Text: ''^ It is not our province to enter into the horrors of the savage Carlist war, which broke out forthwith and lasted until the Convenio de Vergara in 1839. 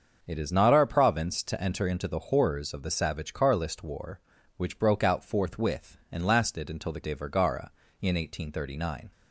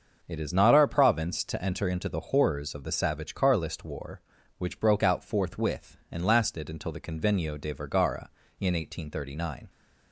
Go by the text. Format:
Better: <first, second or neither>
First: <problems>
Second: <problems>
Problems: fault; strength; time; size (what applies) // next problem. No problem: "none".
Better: second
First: starts louder than the rest; until 1.2 s; 7 dB // skips "Convenio"; at 7.0 s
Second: starts louder than the rest; until 1.2 s; 6.5 dB